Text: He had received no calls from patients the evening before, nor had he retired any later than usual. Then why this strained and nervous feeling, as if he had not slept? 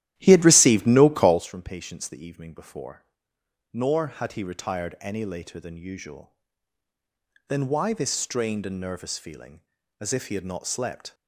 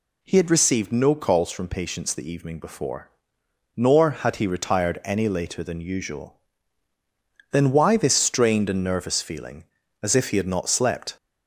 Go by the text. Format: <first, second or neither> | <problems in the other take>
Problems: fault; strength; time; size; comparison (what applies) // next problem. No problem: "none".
second | starts louder than the rest; strong; until 1.5 s; 13 dB